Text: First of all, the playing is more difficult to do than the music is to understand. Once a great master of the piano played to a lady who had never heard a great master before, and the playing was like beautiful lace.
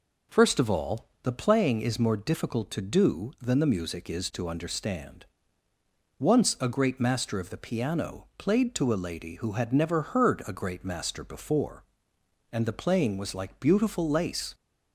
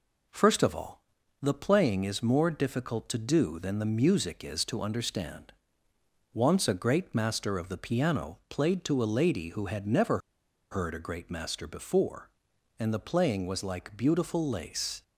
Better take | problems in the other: first | pauses between "never" and "heard"; noticeable; at 10.1 s; 0.53 s long

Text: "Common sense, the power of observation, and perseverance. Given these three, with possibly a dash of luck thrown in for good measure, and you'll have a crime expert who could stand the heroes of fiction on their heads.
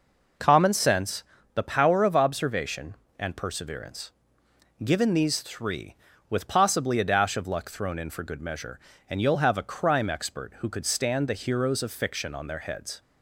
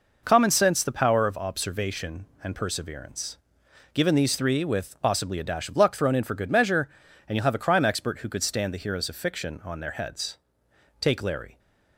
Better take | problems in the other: first | goes on to say "Take Larry"; from 10.9 s on; 0.60 s long

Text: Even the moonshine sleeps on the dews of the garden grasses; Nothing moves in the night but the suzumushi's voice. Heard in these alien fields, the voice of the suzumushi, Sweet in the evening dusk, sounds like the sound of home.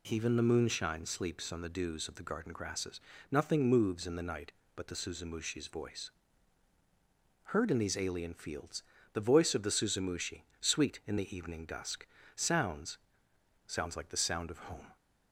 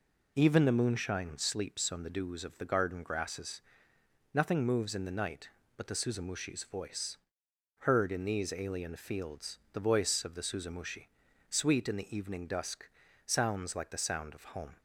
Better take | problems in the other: second | says "sounds" twice; at 13.6 s

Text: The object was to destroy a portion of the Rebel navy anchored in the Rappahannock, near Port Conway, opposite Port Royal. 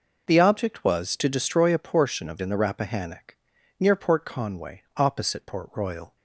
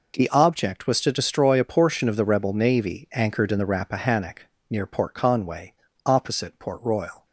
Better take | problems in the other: second | skips "the Rebel navy anchored"; at 2.3 s

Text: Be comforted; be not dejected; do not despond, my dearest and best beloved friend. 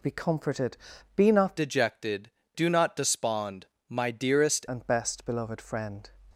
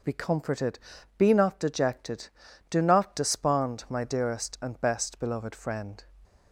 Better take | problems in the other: second | changes voice from "dejected" to "dearest"; from 1.5 to 4.6 s; 3.1 s long

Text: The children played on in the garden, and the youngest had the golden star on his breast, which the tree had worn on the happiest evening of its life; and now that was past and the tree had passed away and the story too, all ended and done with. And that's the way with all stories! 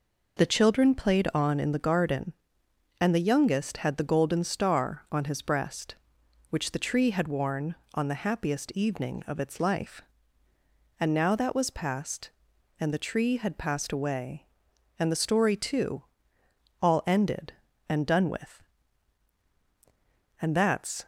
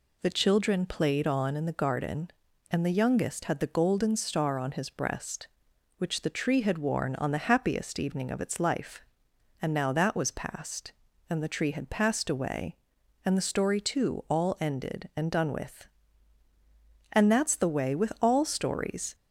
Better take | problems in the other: second | stops before "the way with all stories"; at 21.0 s

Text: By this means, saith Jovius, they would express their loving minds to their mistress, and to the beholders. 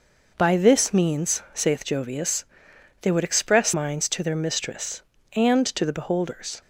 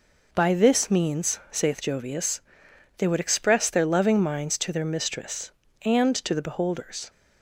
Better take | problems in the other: second | skips "their loving"; at 3.7 s

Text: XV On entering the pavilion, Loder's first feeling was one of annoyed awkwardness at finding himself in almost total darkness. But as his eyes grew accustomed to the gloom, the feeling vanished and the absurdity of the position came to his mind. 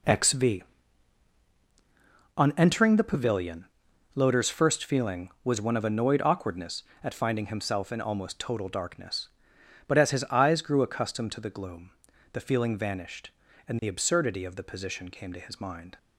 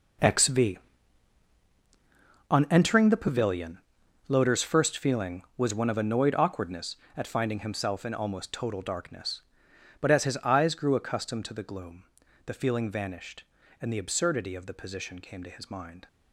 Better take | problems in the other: first | gets quieter; strong; throughout; 13.5 dB

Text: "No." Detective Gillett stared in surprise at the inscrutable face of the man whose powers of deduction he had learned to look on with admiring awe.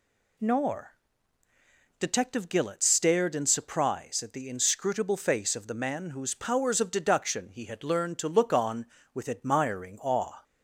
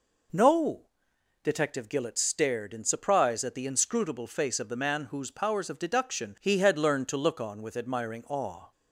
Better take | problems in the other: second | says "Nor" for "No"; at 0.3 s

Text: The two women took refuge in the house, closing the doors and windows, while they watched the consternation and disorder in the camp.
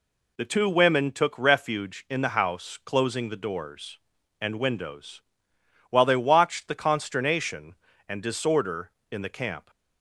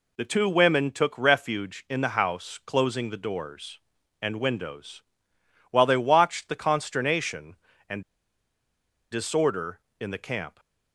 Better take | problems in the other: first | pauses between "and" and "disorder"; at 8.0 s; 1.0 s long

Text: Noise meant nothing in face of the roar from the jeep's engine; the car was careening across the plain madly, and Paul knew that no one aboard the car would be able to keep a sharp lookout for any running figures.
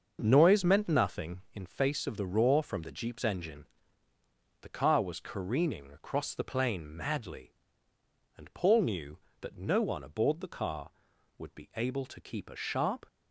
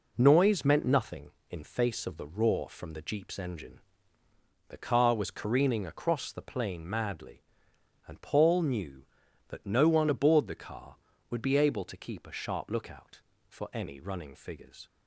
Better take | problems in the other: second | starts louder than the rest; until 1.2 s; 6.5 dB // stops before "lookout for any running figures"; at 13.0 s

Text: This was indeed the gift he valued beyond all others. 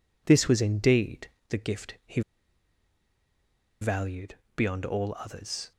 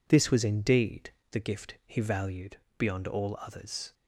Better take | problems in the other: second | pauses between "indeed" and "the"; slight; at 1.2 s; 0.22 s long; slight in the second // pauses between "he" and "valued"; strong; at 2.2 s; 1.6 s long // pauses between "valued" and "beyond"; slight; at 4.3 s; 0.20 s long; slight in the second

